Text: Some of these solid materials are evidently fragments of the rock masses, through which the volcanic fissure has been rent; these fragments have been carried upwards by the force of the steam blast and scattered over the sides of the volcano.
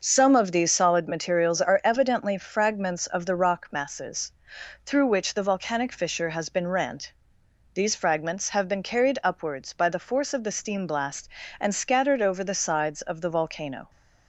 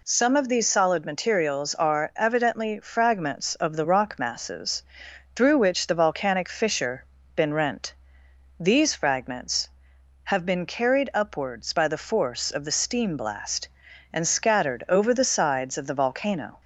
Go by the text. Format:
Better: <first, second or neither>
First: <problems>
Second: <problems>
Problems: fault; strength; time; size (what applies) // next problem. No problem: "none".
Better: first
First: none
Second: skips "has"; at 7.1 s